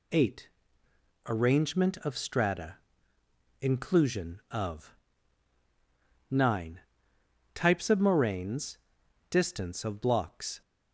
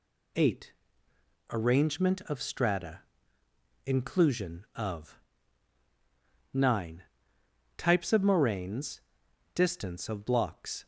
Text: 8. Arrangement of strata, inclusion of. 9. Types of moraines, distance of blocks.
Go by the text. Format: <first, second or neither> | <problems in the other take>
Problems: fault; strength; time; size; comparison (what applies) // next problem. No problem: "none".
neither | none